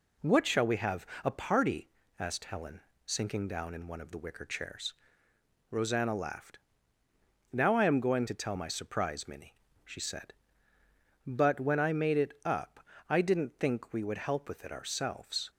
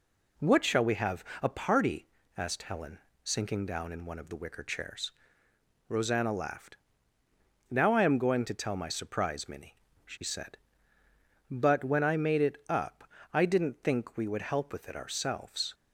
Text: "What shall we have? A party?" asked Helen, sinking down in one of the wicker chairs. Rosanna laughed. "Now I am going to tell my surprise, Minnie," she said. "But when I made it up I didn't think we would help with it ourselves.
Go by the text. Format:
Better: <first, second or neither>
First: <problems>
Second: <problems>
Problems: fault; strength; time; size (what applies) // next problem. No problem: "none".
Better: neither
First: pauses between "up" and "I"; slight; at 12.7 s; 0.30 s long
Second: pauses between "up" and "I"; slight; at 13.0 s; 0.30 s long